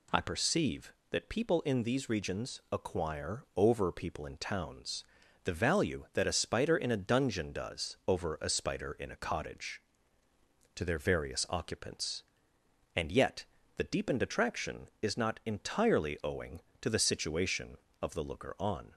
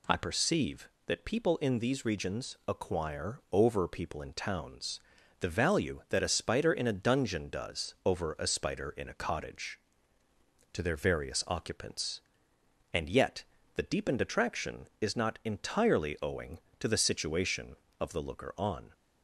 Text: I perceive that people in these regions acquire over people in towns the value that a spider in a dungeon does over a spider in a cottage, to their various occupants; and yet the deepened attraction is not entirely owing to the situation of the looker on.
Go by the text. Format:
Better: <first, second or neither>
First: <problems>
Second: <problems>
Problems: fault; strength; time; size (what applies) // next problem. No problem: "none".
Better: neither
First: pauses between "towns" and "the"; at 5.0 s; 0.40 s long // pauses between "yet" and "the"; slight; at 13.4 s; 0.30 s long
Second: pauses between "towns" and "the"; at 4.9 s; 0.40 s long // pauses between "yet" and "the"; slight; at 13.4 s; 0.30 s long